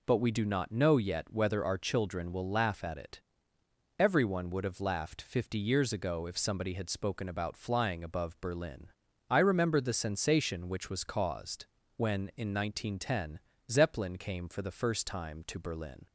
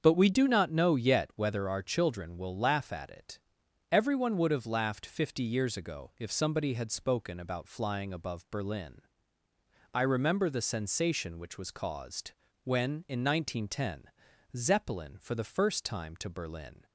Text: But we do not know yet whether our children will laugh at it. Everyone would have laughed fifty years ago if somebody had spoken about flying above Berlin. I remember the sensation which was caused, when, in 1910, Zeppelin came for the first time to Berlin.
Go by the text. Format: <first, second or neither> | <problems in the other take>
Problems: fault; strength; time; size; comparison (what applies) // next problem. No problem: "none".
first | starts louder than the rest; until 1.0 s; 7 dB // skips "came"; at 15.1 s